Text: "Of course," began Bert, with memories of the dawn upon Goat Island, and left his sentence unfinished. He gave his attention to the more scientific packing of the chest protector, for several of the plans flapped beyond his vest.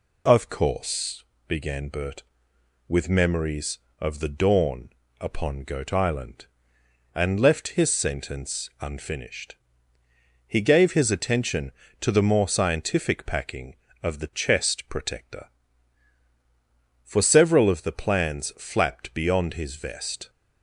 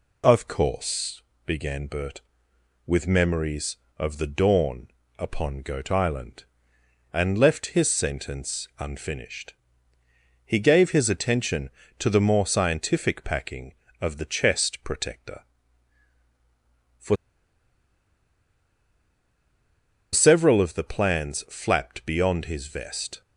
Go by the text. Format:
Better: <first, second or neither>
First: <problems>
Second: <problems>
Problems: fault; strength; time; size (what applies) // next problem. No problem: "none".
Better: first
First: pauses between "dawn" and "upon"; slight; at 4.9 s; 0.30 s long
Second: pauses between "dawn" and "upon"; slight; at 4.8 s; 0.30 s long // pauses between "for" and "several"; strong; at 17.1 s; 2.9 s long